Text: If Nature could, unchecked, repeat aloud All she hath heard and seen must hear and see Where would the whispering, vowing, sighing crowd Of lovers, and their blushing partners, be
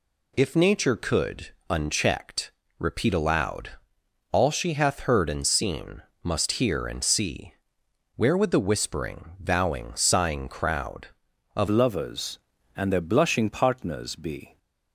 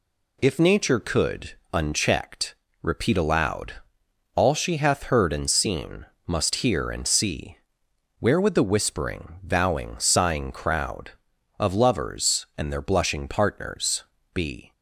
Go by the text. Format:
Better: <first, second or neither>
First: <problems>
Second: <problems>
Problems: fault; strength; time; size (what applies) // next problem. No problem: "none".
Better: second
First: pauses between "aloud" and "All"; noticeable; at 3.7 s; 0.62 s long // pauses between "seen" and "must"; slight; at 6.0 s; 0.22 s long // pauses between "see" and "Where"; noticeable; at 7.5 s; 0.62 s long // changes voice at "lovers"; from 11.6 s on; 2.9 s long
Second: pauses between "aloud" and "All"; noticeable; at 3.7 s; 0.62 s long // pauses between "seen" and "must"; slight; at 6.0 s; 0.22 s long // pauses between "see" and "Where"; noticeable; at 7.5 s; 0.62 s long